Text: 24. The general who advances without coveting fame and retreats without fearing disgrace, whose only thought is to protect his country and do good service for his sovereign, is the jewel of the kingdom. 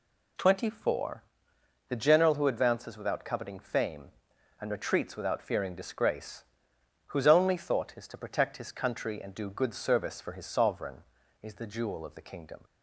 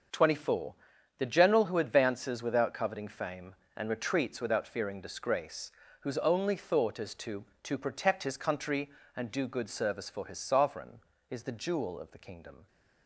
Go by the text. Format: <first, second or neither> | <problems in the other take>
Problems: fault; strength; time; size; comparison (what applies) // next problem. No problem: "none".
first | starts louder than the rest; until 1.5 s; 6 dB // says "to" twice; at 7.6 s